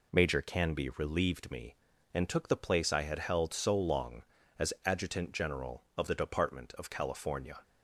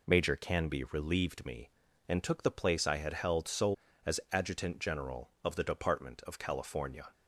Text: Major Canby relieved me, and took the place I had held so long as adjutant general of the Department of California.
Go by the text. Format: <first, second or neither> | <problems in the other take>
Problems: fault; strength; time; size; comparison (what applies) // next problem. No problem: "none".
first | skips "long"; at 3.8 s